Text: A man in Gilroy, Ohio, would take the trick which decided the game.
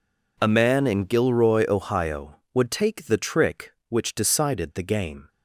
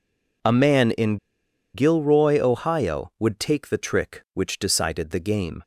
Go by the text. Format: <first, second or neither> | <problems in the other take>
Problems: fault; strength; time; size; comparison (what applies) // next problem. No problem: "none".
first | pauses between "in" and "Gilroy"; noticeable; at 1.1 s; 0.56 s long